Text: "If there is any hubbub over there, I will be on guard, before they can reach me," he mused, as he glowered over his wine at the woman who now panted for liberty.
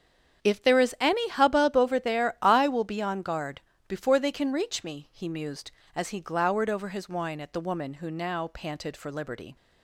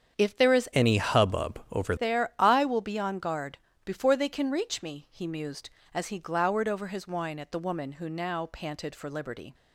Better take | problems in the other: first | starts louder than the rest; strong; until 1.2 s; 8 dB; strong in the first // changes voice from "any" to "over"; from 0.7 to 1.9 s; 1.2 s long

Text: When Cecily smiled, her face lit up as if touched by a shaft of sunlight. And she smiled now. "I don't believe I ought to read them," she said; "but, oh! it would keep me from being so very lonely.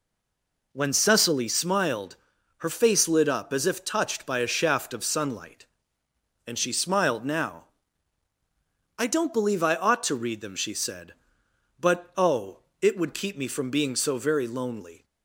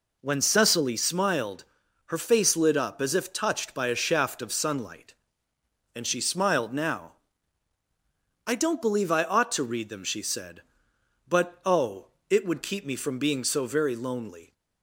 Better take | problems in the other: second | stays silent before the first word; slight; until 0.7 s; 0.7 s long

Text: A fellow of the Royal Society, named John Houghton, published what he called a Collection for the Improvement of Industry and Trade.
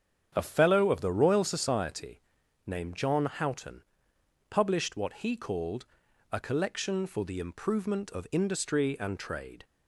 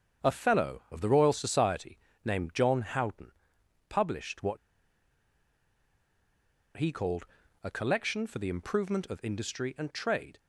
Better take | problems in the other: first | starts louder than the rest; strong; until 1.3 s; 7.5 dB; strong in the first // pauses between "what" and "he"; strong; at 4.5 s; 2.2 s long // pauses between "called" and "a"; at 7.2 s; 0.38 s long; noticeable in the first

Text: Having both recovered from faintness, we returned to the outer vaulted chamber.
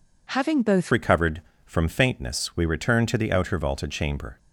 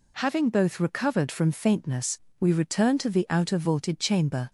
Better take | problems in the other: second | changes voice at "recovered"; from 0.9 s on; 3.4 s long

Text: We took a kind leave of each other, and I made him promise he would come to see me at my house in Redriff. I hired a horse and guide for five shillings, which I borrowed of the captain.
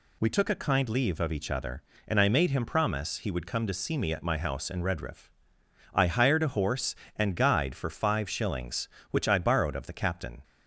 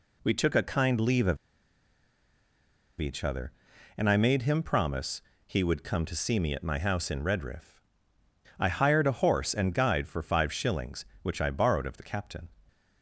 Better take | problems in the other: first | pauses between "of" and "each"; strong; at 1.3 s; 1.6 s long // pauses between "promise" and "he"; slight; at 5.2 s; 0.24 s long

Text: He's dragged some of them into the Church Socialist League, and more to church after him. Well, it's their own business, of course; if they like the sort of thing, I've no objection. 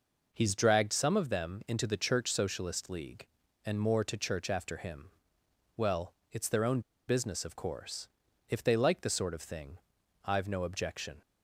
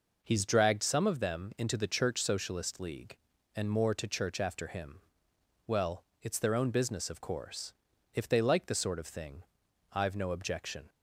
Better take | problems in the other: second | pauses between "own" and "business"; slight; at 6.7 s; 0.28 s long

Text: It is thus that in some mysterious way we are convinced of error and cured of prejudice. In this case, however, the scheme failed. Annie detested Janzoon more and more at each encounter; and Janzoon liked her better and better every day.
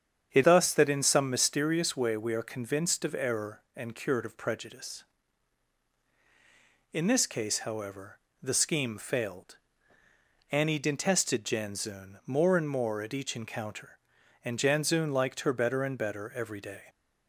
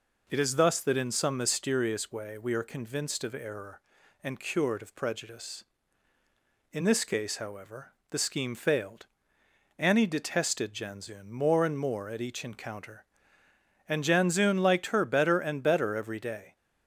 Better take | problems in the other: second | starts louder than the rest; strong; until 1.3 s; 8 dB // skips "is"; at 0.4 s

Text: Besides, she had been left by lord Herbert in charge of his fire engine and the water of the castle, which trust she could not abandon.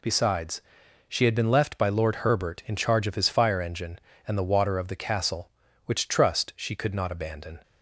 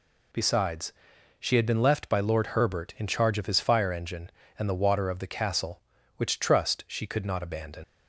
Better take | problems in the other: first | leaves "abandon" unfinished; at 7.8 s; 95 ms

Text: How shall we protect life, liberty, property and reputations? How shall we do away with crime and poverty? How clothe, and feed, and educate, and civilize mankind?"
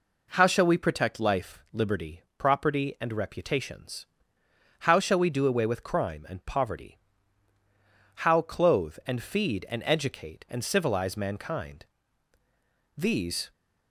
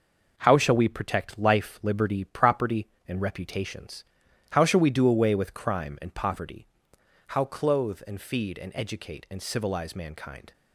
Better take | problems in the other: second | goes on to say "These"; from 12.9 s on; 0.56 s long

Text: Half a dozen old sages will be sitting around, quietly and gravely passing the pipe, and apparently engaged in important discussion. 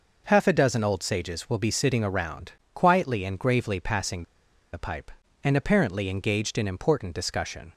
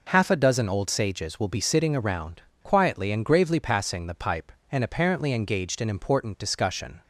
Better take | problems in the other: second | pauses between "passing" and "the"; noticeable; at 4.2 s; 0.49 s long

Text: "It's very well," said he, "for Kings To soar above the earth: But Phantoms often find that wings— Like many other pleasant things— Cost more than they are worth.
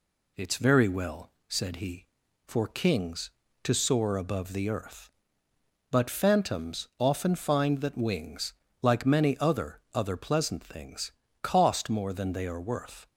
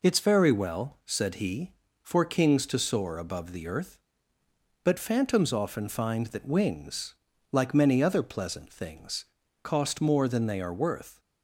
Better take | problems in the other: second | says "other" twice; at 9.9 s

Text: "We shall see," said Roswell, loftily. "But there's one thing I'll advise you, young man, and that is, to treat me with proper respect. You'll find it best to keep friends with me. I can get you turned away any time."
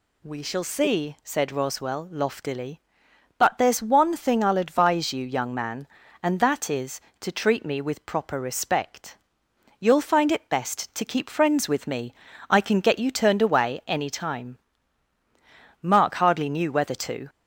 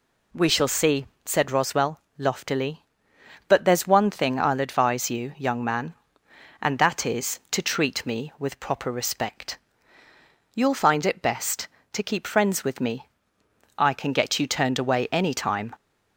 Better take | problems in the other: second | goes on to say "Mark hardly knew whether to"; from 15.8 s on; 1.4 s long

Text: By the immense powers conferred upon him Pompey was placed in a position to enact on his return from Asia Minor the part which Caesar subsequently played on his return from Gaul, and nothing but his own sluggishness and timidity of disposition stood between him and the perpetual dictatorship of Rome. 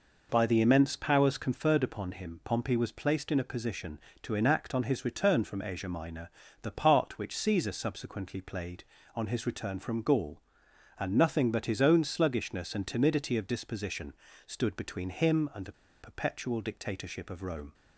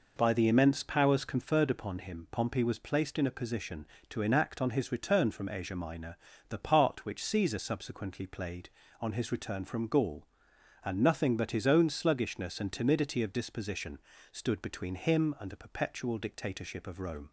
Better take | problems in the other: second | pauses between "Minor" and "the"; slight; at 6.3 s; 0.32 s long; slight in the second // pauses between "disposition" and "stood"; slight; at 14.1 s; 0.32 s long; slight in the second // pauses between "the" and "perpetual"; slight; at 15.7 s; 0.29 s long

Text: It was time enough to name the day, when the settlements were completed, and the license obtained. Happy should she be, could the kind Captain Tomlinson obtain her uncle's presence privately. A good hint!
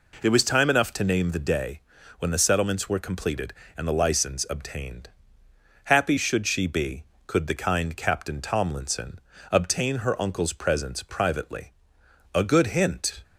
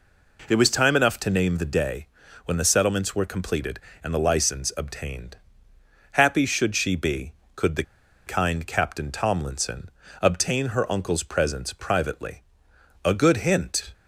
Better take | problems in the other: first | pauses between "the" and "kind"; at 7.8 s; 0.42 s long // pauses between "Tomlinson" and "obtain"; slight; at 9.8 s; 0.30 s long; slight in the first

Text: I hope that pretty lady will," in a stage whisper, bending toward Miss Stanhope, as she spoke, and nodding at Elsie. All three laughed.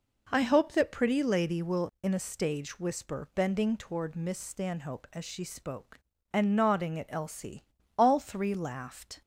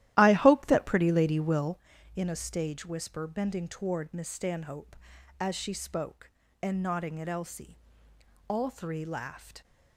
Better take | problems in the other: first | starts louder than the rest; strong; until 1.8 s; 13.5 dB

